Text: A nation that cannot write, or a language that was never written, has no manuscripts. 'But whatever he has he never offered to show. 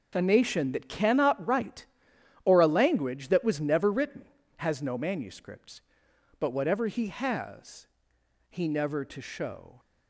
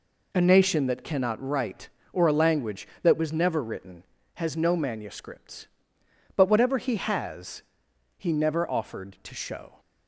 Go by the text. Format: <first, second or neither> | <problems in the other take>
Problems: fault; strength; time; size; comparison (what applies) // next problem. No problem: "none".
second | pauses between "has" and "he"; noticeable; at 7.8 s; 0.60 s long; noticeable in the second // skips "offered"; at 9.0 s